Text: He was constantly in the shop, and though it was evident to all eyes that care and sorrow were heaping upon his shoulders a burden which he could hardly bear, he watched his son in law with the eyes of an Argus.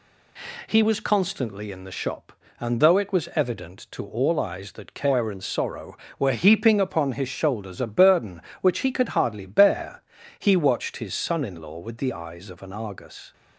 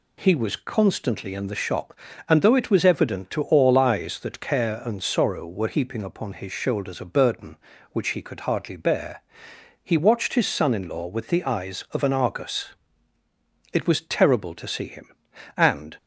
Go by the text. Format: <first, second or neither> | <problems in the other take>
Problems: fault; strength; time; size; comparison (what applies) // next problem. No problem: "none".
first | goes on to say "It was terrible to see him and"; strong; from 13.7 s on; 2.2 s long